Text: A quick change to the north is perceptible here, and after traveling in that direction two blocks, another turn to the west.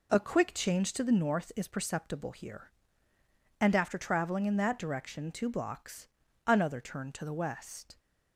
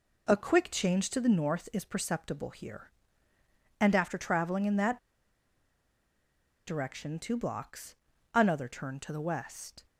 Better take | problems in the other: first | pauses between "that" and "direction"; strong; at 4.9 s; 1.6 s long

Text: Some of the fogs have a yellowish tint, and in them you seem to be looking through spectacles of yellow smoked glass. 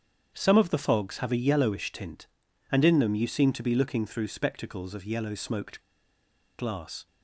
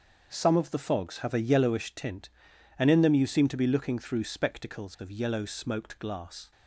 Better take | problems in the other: second | starts louder than the rest; strong; until 1.3 s; 8 dB; also in the second // pauses between "smoked" and "glass"; noticeable; at 5.8 s; 0.77 s long

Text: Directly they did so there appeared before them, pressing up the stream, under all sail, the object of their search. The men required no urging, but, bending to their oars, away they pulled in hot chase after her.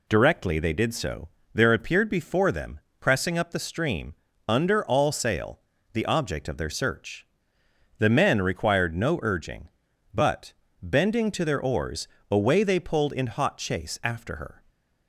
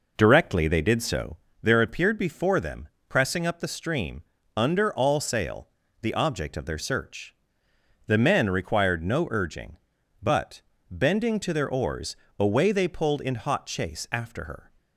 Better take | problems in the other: first | starts louder than the rest; noticeable; until 1.3 s; 4.5 dB // pauses between "so" and "there"; slight; at 1.3 s; 0.24 s long; slight in the first

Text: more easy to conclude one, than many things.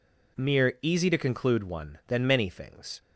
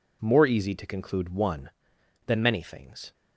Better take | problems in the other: second | says "mere" for "more"; at 0.3 s

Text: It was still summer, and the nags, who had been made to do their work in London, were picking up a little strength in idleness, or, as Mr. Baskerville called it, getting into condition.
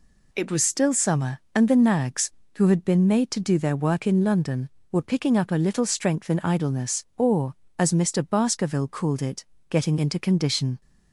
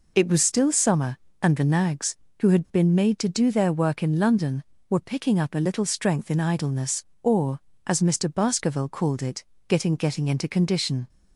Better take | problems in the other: first | says "getting" twice; at 9.9 s

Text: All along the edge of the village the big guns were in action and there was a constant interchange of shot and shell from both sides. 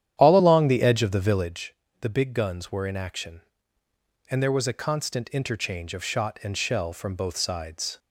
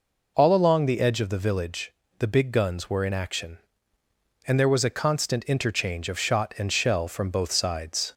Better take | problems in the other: second | starts louder than the rest; strong; until 1.6 s; 10.5 dB // pauses between "village" and "the"; slight; at 1.7 s; 0.26 s long; slight in the second

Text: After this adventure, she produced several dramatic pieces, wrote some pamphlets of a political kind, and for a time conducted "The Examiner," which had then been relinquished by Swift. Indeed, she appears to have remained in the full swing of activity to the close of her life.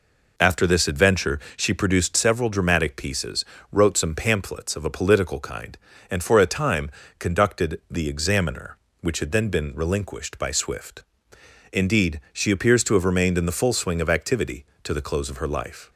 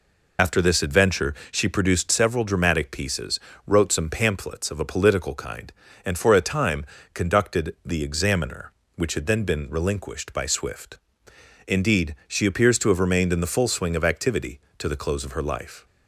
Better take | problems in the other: first | loses the start of "After"; at 0.3 s; 60 ms // pauses between "time" and "conducted"; slight; at 6.8 s; 0.28 s long; slight in the first

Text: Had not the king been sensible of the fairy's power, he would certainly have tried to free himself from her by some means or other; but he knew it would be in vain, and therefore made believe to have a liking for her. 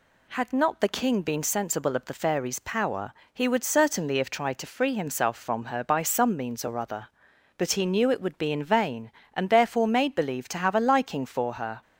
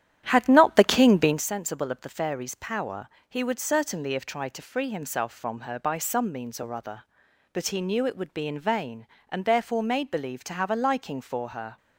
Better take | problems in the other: first | starts louder than the rest; strong; until 1.4 s; 11 dB

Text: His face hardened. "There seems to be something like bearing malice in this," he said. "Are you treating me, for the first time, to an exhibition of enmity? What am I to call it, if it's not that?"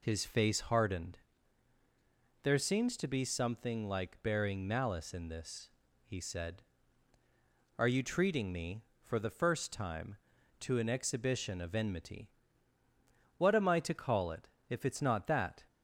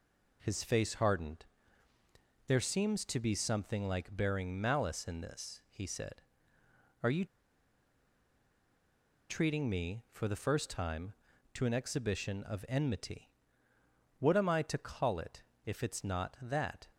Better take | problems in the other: first | pauses between "you" and "treating"; strong; at 7.2 s; 2.0 s long

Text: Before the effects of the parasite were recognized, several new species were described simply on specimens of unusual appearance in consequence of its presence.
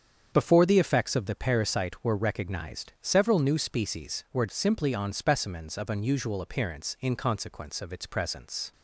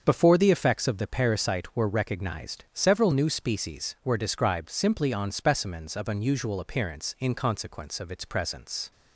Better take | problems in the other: second | starts louder than the rest; strong; until 1.3 s; 7.5 dB; also in the second // skips "described"; at 4.4 s

